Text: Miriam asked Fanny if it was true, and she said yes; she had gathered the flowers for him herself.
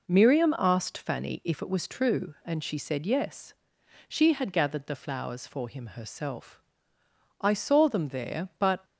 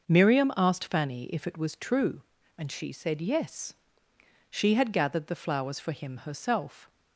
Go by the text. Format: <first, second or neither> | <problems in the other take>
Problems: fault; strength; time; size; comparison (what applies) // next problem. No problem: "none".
second | goes on to say "I saw them there but"; from 7.3 s on; 1.4 s long